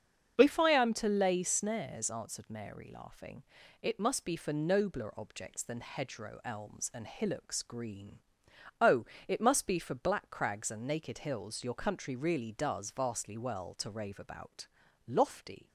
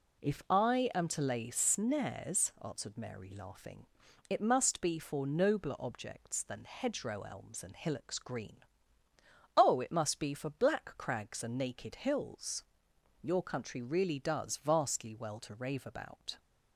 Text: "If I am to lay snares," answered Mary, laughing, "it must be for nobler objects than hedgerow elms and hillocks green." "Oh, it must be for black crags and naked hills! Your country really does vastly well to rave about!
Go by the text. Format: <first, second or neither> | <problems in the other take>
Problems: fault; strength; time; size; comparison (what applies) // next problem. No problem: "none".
second | starts louder than the rest; until 1.4 s; 7 dB // goes on to say "Lofty"; noticeable; from 15.0 s on; 0.62 s long